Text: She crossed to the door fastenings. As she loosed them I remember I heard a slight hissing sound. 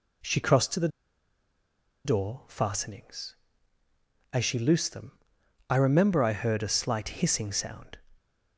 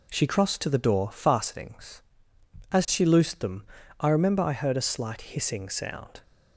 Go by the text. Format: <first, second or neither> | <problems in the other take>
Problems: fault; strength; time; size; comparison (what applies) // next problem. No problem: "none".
second | pauses between "the" and "door"; at 0.8 s; 1.1 s long // pauses between "them" and "I"; noticeable; at 5.1 s; 0.56 s long; slight in the second